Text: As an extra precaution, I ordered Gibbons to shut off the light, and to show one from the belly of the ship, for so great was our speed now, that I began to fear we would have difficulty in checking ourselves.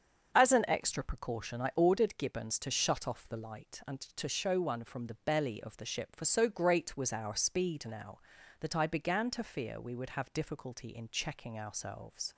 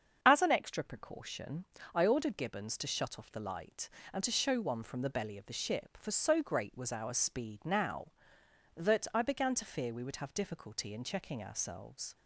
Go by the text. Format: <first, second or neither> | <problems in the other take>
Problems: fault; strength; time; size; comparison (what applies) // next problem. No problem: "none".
neither | starts louder than the rest; the same in both